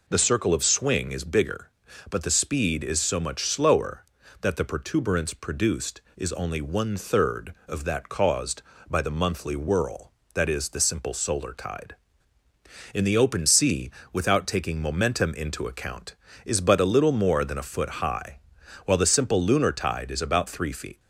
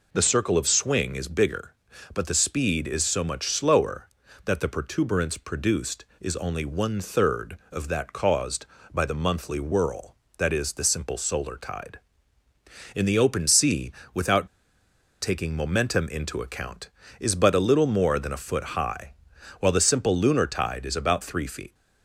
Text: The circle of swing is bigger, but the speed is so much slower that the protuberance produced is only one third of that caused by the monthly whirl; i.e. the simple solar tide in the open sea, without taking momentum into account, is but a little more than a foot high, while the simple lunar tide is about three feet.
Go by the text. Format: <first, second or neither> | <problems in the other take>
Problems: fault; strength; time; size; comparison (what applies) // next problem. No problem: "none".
first | pauses between "without" and "taking"; noticeable; at 14.4 s; 0.74 s long